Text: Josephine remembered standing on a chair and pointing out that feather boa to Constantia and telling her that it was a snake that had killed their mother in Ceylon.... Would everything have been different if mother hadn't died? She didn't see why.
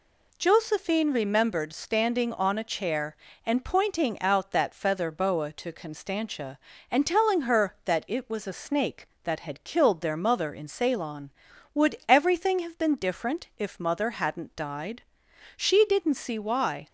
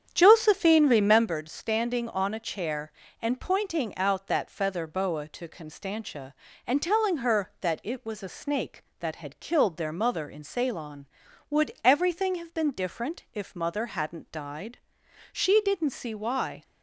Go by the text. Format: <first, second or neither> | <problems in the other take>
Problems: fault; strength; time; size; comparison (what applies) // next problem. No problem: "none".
first | starts louder than the rest; strong; until 1.4 s; 8.5 dB